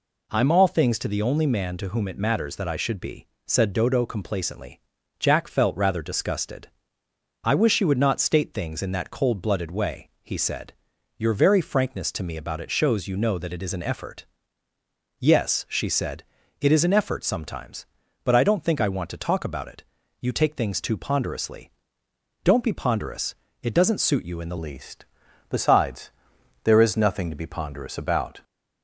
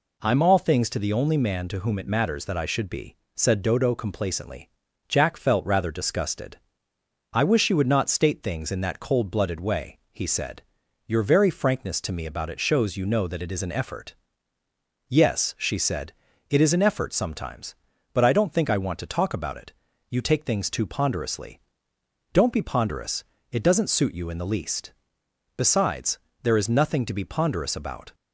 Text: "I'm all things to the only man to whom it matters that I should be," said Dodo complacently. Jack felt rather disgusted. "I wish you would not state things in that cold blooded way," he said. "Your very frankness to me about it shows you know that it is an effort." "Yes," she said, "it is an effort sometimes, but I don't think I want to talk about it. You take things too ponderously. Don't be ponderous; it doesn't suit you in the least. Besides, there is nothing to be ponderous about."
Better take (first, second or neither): second